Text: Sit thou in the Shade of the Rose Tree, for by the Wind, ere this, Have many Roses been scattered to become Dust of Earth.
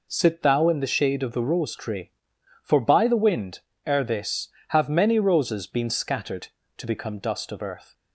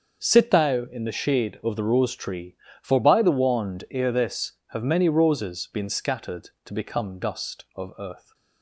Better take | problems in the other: first | starts louder than the rest; until 1.3 s; 6.5 dB // says "Wand" for "Wind"; at 3.3 s

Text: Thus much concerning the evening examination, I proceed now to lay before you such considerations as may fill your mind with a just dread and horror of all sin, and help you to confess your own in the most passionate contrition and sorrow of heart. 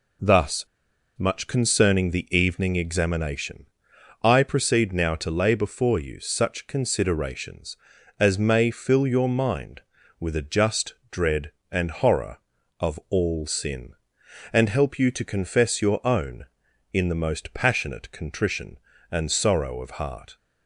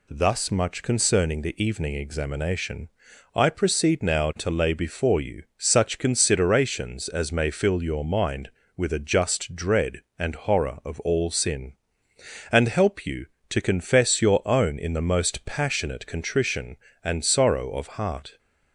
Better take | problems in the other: second | pauses between "Thus" and "much"; noticeable; at 0.6 s; 0.50 s long // pauses between "just" and "dread"; slight; at 10.9 s; 0.18 s long

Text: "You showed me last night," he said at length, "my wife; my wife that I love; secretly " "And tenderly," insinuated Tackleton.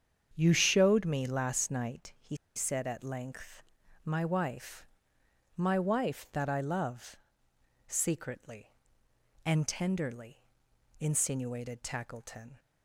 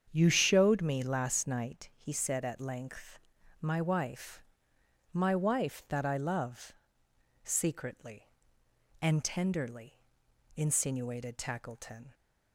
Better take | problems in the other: second | starts louder than the rest; strong; until 1.3 s; 7.5 dB; strong in the second // pauses between "he" and "said"; slight; at 2.3 s; 0.19 s long

